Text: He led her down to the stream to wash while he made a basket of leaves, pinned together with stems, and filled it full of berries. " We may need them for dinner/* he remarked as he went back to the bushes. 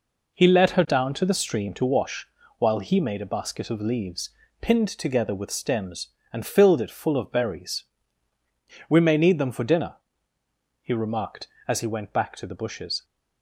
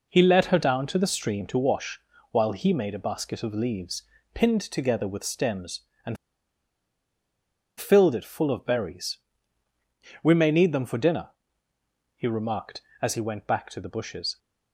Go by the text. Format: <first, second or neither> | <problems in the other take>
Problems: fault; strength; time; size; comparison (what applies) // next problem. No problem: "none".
first | pauses between "wash" and "while"; slight; at 2.0 s; 0.30 s long; slight in the first // pauses between "and" and "filled"; strong; at 6.1 s; 1.6 s long